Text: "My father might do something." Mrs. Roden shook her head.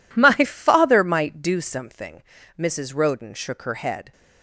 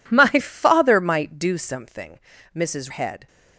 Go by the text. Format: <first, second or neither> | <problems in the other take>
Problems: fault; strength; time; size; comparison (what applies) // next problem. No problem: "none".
first | skips "Roden shook her"; at 2.9 s